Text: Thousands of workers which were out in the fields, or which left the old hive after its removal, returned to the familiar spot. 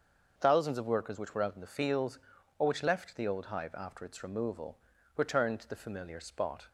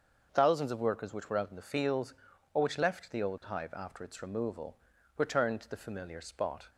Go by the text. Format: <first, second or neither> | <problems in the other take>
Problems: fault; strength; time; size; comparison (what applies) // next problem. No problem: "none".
neither | starts louder than the rest; the same in both